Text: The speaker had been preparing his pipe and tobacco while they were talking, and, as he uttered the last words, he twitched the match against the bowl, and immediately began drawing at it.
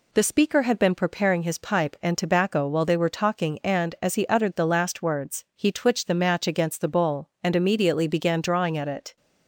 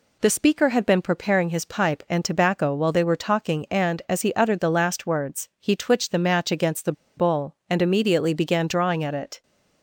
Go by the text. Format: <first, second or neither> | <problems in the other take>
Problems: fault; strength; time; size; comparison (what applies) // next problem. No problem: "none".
first | pauses between "the" and "bowl"; slight; at 6.9 s; 0.25 s long